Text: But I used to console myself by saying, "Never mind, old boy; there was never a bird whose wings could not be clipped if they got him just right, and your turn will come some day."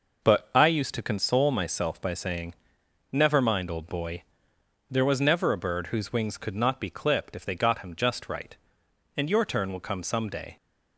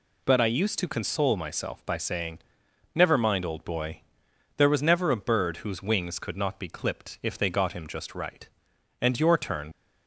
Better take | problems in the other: first | stops before "will come some day"; at 9.7 s

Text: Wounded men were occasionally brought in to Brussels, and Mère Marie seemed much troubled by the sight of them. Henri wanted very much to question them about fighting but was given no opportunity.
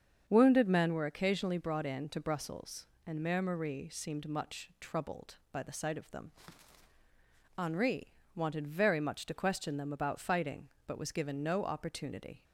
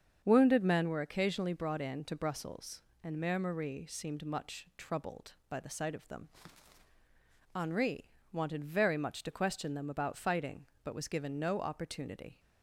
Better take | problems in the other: neither | starts louder than the rest; the same in both // pauses between "Henri" and "wanted"; slight; the same in both

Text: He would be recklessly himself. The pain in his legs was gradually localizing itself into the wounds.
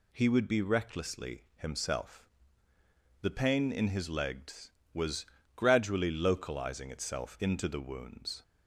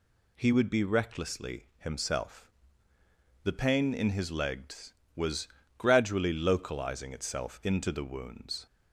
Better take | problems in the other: neither | pauses between "was" and "gradually"; slight; the same in both

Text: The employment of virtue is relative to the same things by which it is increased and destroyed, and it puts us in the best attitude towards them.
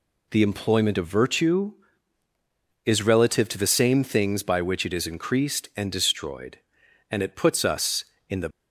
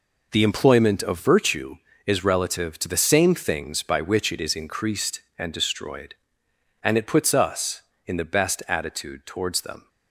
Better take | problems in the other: second | stops before "best attitude towards them"; at 8.5 s

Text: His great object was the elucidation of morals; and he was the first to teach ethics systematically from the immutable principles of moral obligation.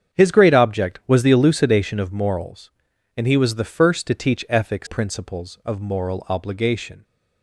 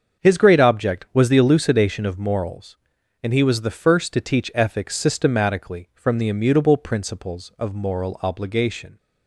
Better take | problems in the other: second | starts louder than the rest; strong; until 1.2 s; 8 dB; also in the second // skips "systematically from the immutable"; at 4.8 s

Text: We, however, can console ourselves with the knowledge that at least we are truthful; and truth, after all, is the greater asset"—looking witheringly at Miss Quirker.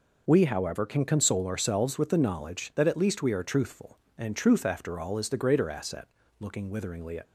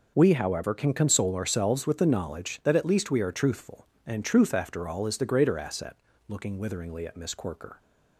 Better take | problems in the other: second | stops before "Miss Quirker"; at 7.2 s

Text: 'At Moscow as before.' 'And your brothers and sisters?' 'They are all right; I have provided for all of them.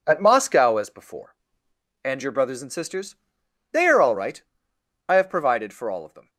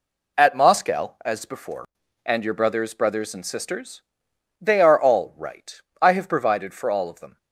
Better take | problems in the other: first | says "brothers" twice; at 2.9 s

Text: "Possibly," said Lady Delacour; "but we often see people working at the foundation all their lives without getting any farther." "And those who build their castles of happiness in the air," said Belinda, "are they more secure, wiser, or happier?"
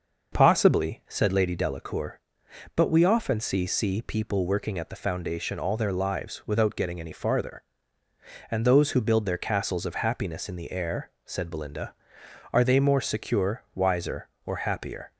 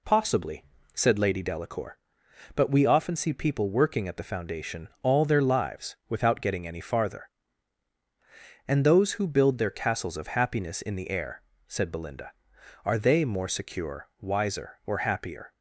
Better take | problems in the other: second | starts louder than the rest; noticeable; until 1.3 s; 6 dB // says "see" twice; at 3.6 s

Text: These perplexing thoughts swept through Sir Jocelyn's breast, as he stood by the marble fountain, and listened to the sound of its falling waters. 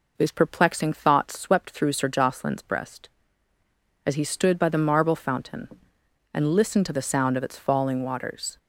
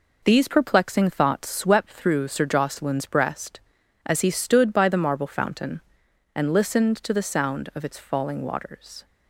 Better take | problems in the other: neither | none

